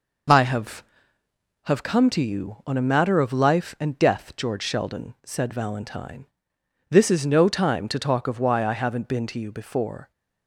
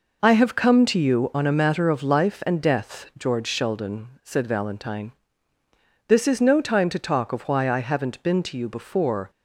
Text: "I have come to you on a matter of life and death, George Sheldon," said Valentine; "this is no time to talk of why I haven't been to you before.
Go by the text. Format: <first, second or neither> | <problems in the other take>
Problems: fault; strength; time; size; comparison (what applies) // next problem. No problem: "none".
second | says "have" twice; at 1.6 s